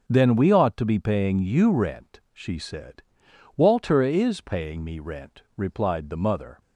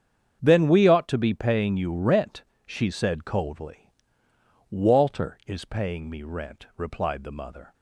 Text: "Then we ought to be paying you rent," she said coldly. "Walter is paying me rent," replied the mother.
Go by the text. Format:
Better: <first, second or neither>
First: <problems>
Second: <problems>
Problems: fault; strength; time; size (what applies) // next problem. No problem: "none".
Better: second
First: starts louder than the rest; until 1.0 s; 6.5 dB // skips "coldly"; at 3.2 s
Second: starts louder than the rest; strong; until 1.4 s; 7.5 dB